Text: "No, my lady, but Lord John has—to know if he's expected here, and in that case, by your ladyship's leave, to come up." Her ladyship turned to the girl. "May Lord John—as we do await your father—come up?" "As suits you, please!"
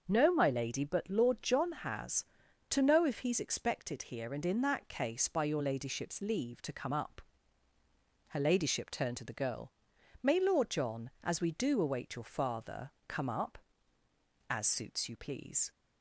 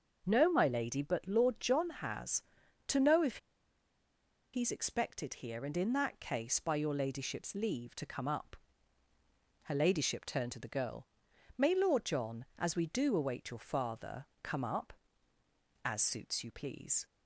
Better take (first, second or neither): first